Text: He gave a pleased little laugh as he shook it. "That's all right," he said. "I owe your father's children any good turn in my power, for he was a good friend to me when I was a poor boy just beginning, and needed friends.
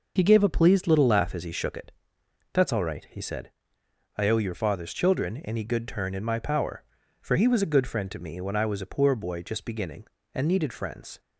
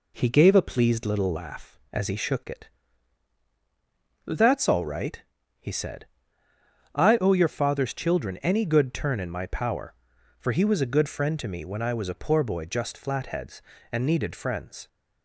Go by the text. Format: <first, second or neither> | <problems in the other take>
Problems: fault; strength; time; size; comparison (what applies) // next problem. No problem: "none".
first | says "flatheads" for "beginning"; at 12.9 s